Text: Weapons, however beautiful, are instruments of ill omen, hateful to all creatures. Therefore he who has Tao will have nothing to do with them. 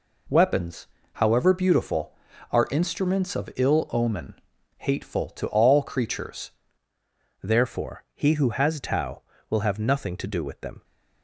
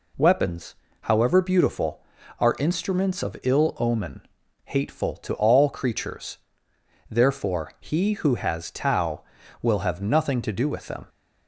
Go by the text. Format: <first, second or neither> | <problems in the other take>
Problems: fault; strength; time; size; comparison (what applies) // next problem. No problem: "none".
second | changes voice at "Therefore"; from 7.4 s on; 3.4 s long